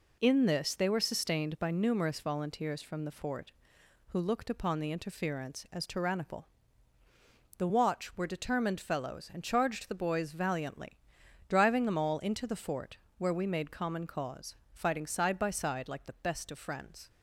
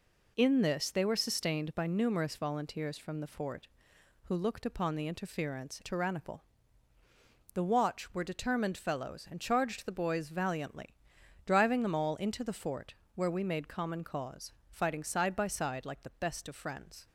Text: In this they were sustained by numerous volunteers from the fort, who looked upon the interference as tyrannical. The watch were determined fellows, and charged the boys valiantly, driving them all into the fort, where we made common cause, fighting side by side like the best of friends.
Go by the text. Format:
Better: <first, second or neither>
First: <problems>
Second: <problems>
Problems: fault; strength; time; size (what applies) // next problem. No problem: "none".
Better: first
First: none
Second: skips "as"; at 5.8 s